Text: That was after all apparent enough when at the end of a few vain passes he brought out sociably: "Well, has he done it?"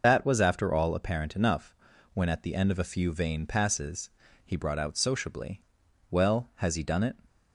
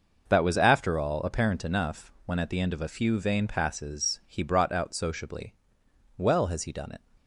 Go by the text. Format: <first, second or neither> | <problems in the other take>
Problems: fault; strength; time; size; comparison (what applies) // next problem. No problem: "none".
second | loses the start of "That"; at 0.0 s; 55 ms // pauses between "enough" and "when"; at 1.7 s; 0.38 s long // pauses between "passes" and "he"; slight; at 4.0 s; 0.36 s long